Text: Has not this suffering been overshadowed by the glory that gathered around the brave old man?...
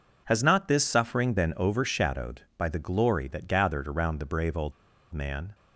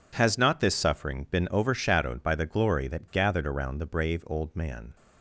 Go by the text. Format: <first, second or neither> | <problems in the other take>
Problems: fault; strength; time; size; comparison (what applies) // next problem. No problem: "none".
second | pauses between "old" and "man"; at 4.7 s; 0.40 s long